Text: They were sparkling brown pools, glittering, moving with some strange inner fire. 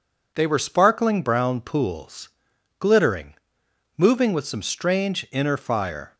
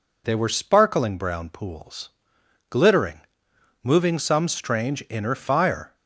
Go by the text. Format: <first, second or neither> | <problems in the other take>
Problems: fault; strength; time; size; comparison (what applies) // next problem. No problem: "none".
first | skips "with"; at 4.1 s